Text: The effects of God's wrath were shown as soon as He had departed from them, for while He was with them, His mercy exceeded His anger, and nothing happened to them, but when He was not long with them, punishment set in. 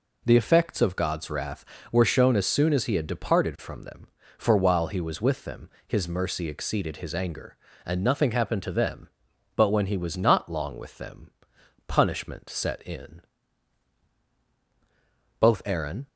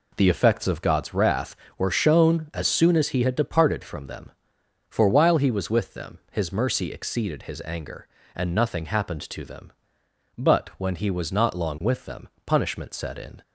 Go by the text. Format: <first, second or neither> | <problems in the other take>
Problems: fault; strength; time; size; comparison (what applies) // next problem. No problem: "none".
second | goes on to say "Both Aaron"; noticeable; from 15.3 s on; 0.68 s long